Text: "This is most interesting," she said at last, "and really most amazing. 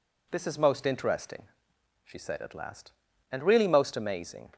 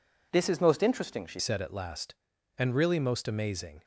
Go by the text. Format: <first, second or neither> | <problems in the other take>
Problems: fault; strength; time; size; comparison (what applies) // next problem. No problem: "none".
first | changes voice at "said"; from 1.3 s on; 2.5 s long